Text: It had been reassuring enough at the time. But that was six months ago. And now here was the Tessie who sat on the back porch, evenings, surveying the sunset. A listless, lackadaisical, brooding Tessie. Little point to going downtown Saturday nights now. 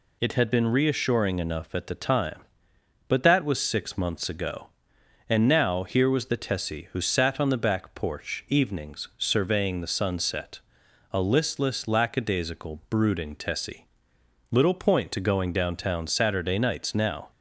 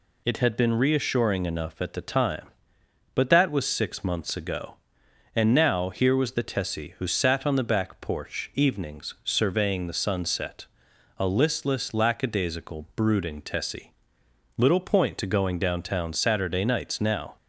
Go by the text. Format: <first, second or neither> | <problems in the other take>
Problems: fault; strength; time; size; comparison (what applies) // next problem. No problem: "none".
neither | none